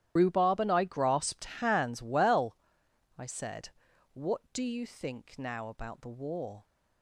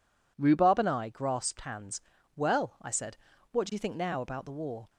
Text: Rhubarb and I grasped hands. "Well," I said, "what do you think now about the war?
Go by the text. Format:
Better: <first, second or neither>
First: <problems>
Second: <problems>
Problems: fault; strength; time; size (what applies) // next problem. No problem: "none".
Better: second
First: loses the start of "Rhubarb"; at 0.1 s; 55 ms // starts louder than the rest; strong; until 1.1 s; 12 dB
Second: none